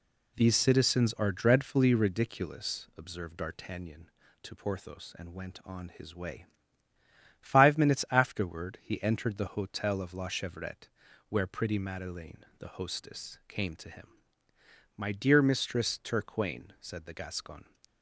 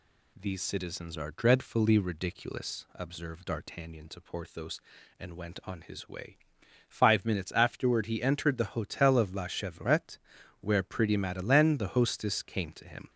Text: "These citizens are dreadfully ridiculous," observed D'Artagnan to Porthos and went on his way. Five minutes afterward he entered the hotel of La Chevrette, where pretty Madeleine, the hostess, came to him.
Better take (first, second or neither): second